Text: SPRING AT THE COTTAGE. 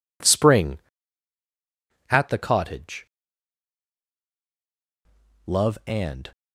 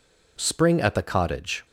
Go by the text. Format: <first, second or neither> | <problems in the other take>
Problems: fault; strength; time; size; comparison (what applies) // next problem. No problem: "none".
second | goes on to say "Love and"; noticeable; from 5.4 s on; 0.84 s long